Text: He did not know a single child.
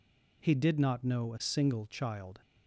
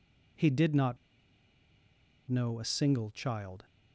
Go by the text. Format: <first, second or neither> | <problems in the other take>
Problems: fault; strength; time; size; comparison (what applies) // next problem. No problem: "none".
first | pauses between "not" and "know"; strong; at 0.9 s; 1.3 s long